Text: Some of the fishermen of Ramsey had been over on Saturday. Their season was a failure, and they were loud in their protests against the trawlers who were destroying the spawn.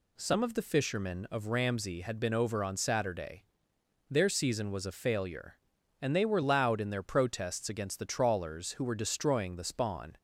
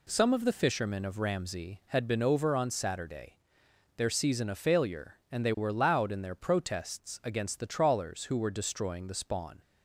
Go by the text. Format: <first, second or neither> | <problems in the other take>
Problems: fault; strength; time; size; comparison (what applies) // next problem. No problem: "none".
first | skips "was"; at 4.4 s